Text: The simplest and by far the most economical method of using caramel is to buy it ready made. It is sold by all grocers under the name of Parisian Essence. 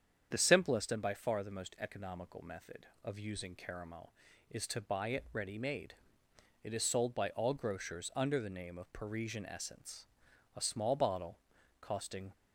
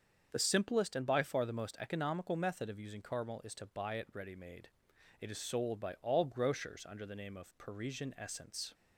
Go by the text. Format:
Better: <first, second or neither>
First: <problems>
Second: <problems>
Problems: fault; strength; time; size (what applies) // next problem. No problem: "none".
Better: second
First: starts louder than the rest; strong; until 1.3 s; 8 dB // goes on to say "A small bottle costing"; strong; from 10.5 s on; 1.7 s long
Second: starts louder than the rest; until 1.3 s; 7 dB